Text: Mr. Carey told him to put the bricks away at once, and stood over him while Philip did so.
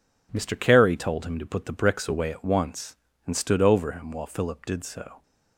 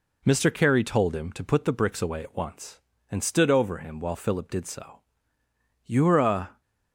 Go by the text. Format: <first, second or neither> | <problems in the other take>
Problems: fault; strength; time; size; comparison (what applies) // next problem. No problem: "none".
first | goes on to say "You're a"; noticeable; from 5.8 s on; 0.78 s long